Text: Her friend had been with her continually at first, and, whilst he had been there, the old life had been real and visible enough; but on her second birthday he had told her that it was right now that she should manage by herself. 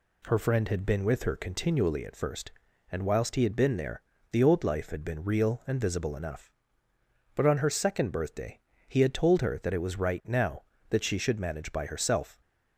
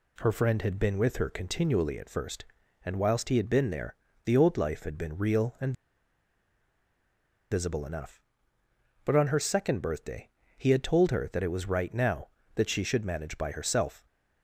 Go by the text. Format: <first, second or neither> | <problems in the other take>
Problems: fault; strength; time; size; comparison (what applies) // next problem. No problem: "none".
first | pauses between "and" and "visible"; strong; at 5.7 s; 1.7 s long // pauses between "birthday" and "he"; slight; at 10.2 s; 0.26 s long; slight in the first